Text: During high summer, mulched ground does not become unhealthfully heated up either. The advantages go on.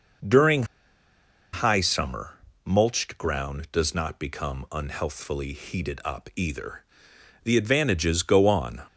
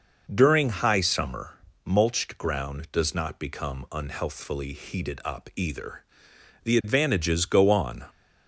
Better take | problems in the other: second | pauses between "During" and "high"; noticeable; at 0.6 s; 0.89 s long

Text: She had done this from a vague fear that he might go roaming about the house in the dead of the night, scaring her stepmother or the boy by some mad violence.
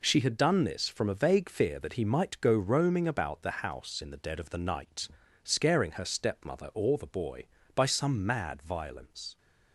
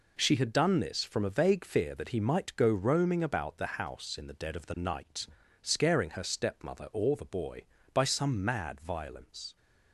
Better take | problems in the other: neither | none

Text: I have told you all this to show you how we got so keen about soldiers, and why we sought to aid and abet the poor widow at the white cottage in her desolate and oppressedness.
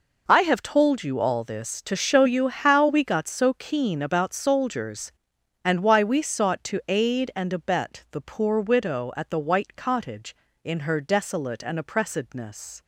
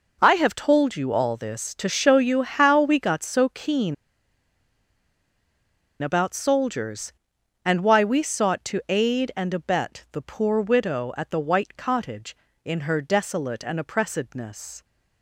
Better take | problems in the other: first | pauses between "keen" and "about"; strong; at 3.9 s; 2.0 s long

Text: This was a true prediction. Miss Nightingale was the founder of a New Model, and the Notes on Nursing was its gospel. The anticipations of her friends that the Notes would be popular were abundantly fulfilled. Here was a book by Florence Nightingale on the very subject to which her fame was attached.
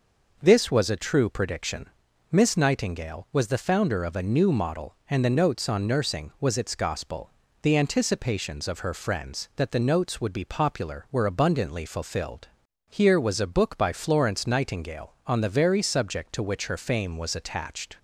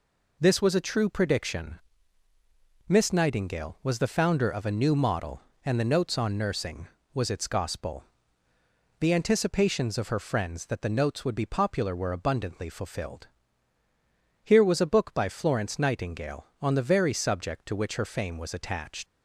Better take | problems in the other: first | leaves "attached" unfinished; at 19.0 s; 95 ms

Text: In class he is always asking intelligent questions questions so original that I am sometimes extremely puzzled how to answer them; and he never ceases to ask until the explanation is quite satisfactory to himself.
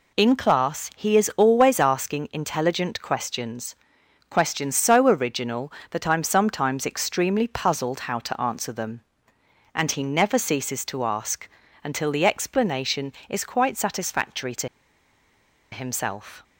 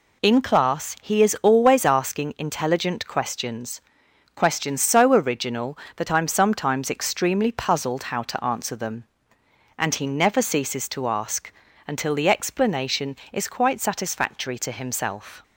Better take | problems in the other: second | pauses between "questions" and "questions"; noticeable; at 3.7 s; 0.54 s long; noticeable in the second // pauses between "ask" and "until"; slight; at 11.4 s; 0.34 s long; slight in the second // pauses between "to" and "himself"; at 14.6 s; 1.0 s long

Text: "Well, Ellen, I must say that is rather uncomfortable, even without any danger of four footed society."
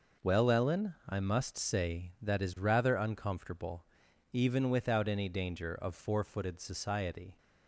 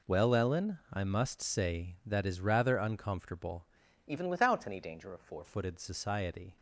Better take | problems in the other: first | changes voice from "even" to "four"; from 4.0 to 5.4 s; 1.4 s long

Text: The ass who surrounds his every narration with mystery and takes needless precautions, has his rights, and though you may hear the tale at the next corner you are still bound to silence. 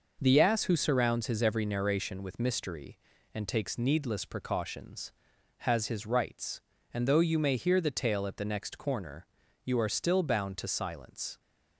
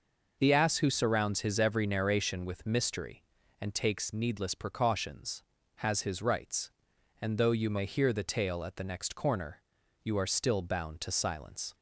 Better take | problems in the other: neither | pauses between "corner" and "you"; the same in both

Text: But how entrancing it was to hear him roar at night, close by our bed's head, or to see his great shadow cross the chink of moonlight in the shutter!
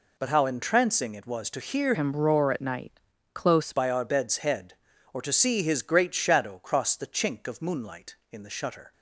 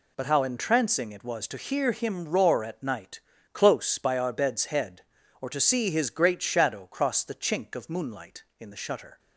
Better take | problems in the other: second | changes voice from "him" to "close"; from 1.9 to 3.7 s; 1.8 s long

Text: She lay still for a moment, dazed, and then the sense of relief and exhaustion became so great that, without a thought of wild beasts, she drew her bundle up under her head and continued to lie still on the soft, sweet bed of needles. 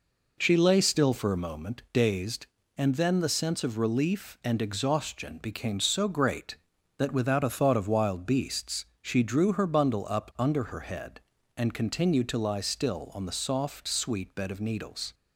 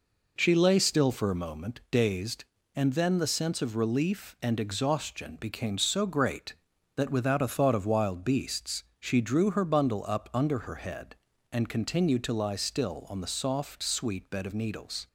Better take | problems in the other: neither | none

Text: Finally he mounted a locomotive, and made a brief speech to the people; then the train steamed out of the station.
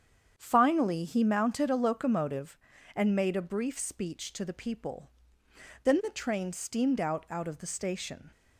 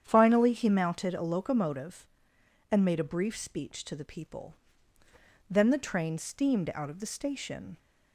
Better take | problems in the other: second | starts louder than the rest; strong; until 1.3 s; 8 dB; strong in the second // says "out" twice; at 7.2 s

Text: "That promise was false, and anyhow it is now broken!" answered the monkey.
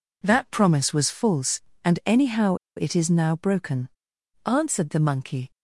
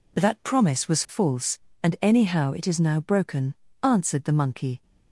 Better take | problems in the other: second | pauses between "anyhow" and "it"; slight; at 2.5 s; 0.20 s long

